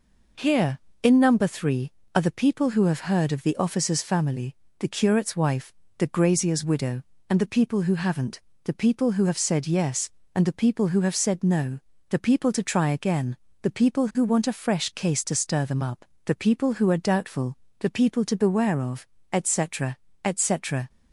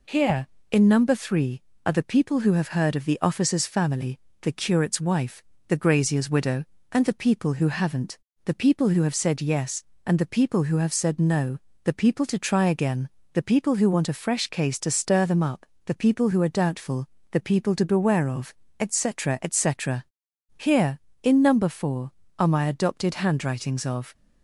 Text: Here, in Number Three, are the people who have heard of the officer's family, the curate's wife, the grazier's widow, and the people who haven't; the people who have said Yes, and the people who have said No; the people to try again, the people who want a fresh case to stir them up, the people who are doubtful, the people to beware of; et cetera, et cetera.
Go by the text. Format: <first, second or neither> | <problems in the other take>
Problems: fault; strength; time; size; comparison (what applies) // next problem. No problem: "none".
first | goes on to say "Here in Number Four are my Adopted Handwritings of"; strong; from 20.5 s on; 3.5 s long